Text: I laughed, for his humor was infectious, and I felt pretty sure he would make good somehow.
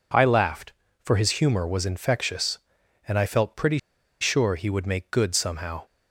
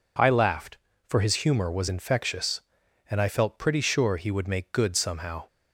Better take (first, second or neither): second